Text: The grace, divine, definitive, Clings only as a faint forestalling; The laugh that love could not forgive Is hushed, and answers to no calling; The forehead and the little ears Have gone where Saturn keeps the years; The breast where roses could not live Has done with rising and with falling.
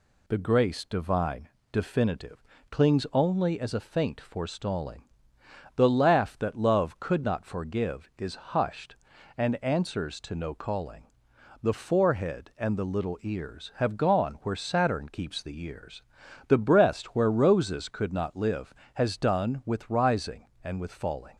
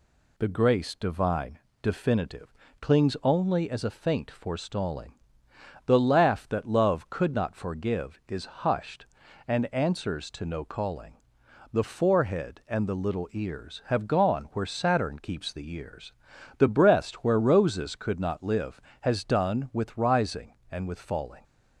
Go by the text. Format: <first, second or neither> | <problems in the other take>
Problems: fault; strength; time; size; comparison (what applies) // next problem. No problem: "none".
neither | none